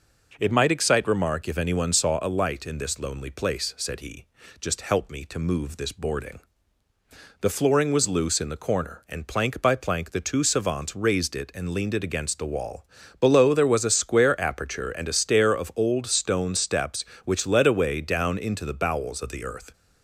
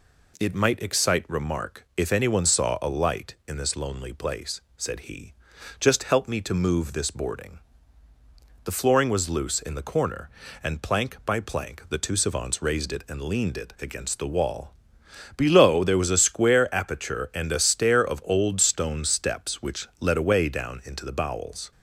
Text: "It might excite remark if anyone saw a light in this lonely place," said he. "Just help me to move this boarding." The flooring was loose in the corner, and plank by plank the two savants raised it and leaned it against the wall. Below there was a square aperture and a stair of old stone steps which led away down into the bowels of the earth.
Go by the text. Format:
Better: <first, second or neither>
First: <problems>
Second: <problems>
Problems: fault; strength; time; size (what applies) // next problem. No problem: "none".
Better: first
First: none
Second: stops before "of the earth"; at 21.7 s